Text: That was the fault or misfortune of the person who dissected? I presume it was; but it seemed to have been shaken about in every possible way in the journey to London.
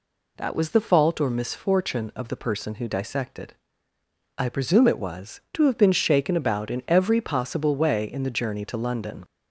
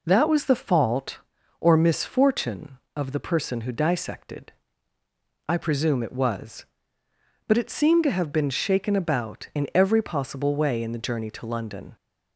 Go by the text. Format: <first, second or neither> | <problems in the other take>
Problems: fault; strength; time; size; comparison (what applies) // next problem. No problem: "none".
second | skips "but it seemed"; at 5.4 s